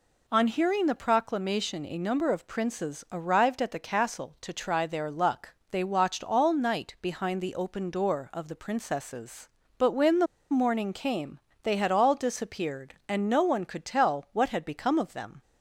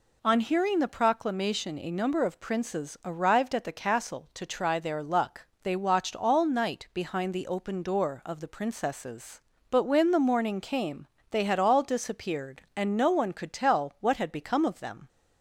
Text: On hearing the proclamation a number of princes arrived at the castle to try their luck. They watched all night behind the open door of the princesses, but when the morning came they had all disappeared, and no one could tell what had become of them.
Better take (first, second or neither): second